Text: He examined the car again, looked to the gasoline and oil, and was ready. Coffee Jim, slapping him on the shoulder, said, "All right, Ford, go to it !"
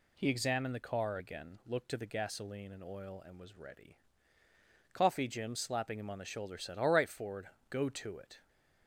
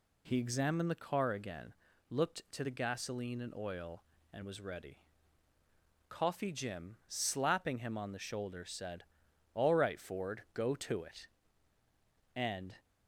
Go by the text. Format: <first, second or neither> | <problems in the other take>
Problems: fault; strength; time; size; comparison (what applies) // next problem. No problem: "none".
first | goes on to say "and"; slight; from 12.3 s on; 0.40 s long